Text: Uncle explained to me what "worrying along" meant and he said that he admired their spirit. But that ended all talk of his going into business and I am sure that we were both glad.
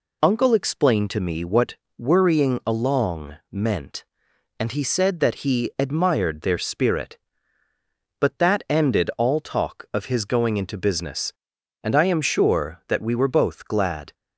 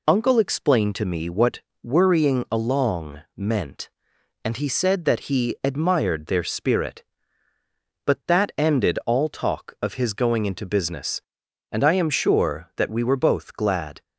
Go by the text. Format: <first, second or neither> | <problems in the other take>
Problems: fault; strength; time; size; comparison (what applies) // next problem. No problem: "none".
neither | pauses between "what" and "worrying"; slight; the same in both // pauses between "along" and "meant"; slight; the same in both